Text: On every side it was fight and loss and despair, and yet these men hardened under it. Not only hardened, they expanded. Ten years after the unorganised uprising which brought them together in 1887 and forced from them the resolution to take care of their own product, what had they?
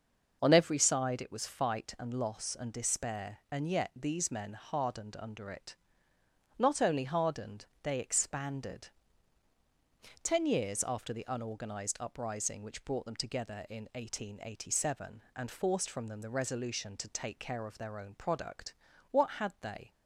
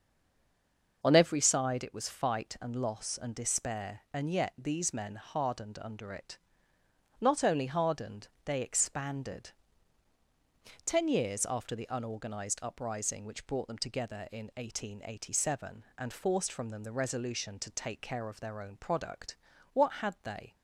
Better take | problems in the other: first | stays silent before the first word; until 1.0 s; 1.0 s long // starts louder than the rest; until 2.0 s; 6 dB; also in the first

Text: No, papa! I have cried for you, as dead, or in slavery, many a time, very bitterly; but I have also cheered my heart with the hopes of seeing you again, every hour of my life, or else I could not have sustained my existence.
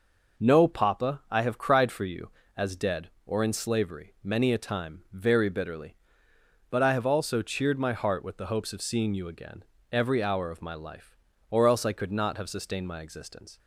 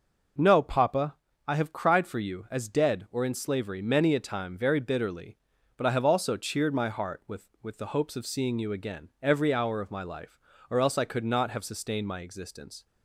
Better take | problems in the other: first | says "with" twice; at 7.6 s

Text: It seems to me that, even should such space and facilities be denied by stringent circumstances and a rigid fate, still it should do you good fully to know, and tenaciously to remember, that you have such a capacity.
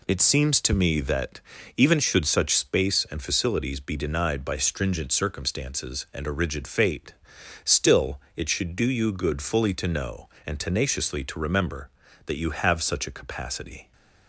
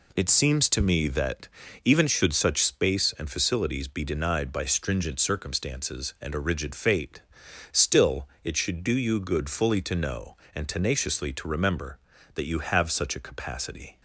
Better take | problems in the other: neither | pauses between "still" and "it"; slight; the same in both

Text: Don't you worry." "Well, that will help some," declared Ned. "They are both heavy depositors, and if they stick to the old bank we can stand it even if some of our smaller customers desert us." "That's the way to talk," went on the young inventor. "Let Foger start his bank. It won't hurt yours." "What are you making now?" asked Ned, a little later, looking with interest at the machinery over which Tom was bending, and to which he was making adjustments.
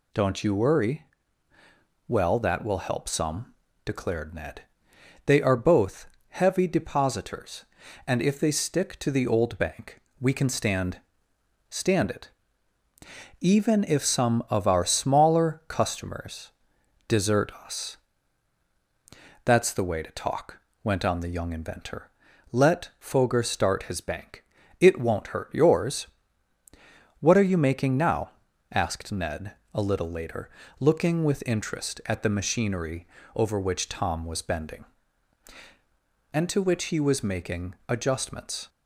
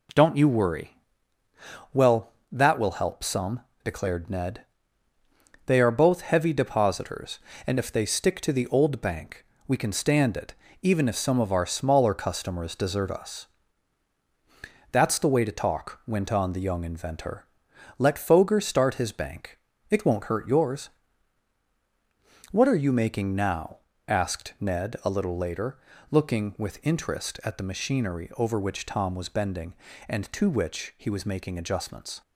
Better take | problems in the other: second | pauses between "both" and "heavy"; slight; at 6.0 s; 0.22 s long // pauses between "bank" and "we"; slight; at 10.0 s; 0.18 s long; slight in the second // says "stand" twice; at 11.7 s // pauses between "it" and "even"; at 12.2 s; 1.1 s long; slight in the second // pauses between "customers" and "desert"; noticeable; at 16.5 s; 0.56 s long // pauses between "machinery" and "over"; slight; at 33.0 s; 0.30 s long

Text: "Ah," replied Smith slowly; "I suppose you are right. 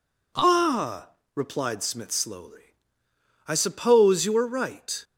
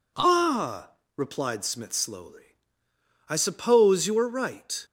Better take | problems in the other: neither | none

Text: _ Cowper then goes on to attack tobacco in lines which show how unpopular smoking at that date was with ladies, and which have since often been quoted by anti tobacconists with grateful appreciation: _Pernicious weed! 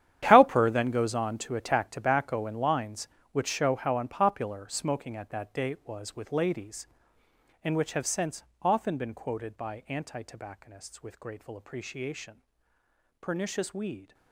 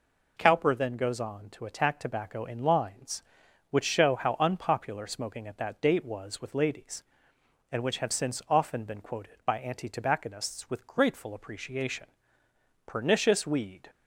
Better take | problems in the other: second | gets quieter; strong; throughout; 15 dB // pauses between "since" and "often"; slight; at 8.4 s; 0.20 s long

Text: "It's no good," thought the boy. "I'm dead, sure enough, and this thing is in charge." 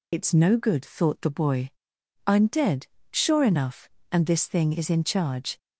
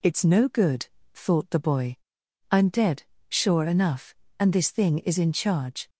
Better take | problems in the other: second | loses the start of "It's"; at 0.1 s; 50 ms

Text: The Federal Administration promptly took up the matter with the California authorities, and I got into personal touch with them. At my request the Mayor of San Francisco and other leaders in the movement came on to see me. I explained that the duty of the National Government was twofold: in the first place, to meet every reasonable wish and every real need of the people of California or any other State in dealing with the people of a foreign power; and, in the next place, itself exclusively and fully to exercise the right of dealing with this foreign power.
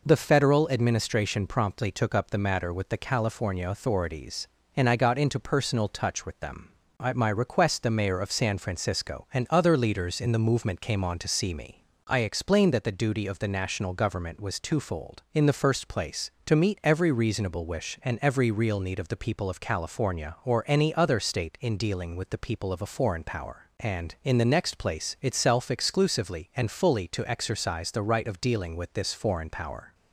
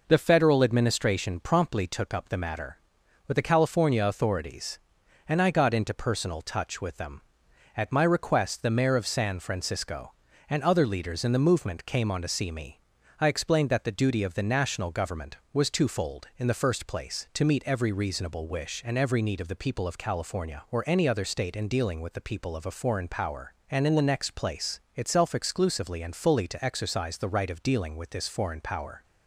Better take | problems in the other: first | skips "real"; at 19.2 s

